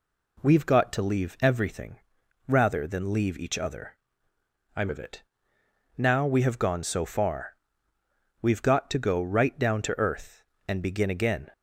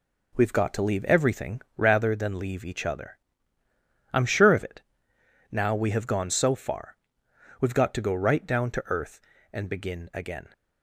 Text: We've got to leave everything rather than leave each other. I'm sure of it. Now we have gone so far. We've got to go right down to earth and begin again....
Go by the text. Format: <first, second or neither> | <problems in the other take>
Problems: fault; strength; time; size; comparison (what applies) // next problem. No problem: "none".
second | pauses between "everything" and "rather"; noticeable; at 1.9 s; 0.50 s long // skips "sure"; at 4.8 s